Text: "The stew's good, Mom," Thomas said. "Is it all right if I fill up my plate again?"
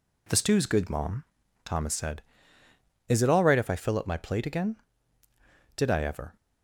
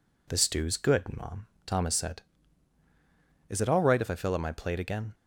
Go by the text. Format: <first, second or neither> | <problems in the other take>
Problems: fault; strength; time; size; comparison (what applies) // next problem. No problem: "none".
second | goes on to say "Did I ever"; from 5.7 s on; 0.60 s long